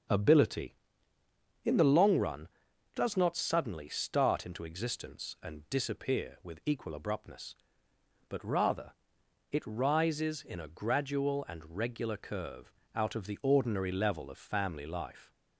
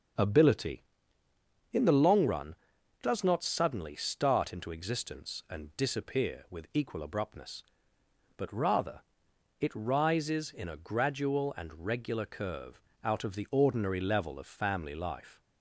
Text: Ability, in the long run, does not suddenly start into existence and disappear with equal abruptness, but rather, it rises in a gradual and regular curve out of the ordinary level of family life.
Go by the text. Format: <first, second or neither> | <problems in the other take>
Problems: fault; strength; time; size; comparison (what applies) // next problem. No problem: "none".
neither | starts louder than the rest; the same in both // pauses between "curve" and "out"; slight; the same in both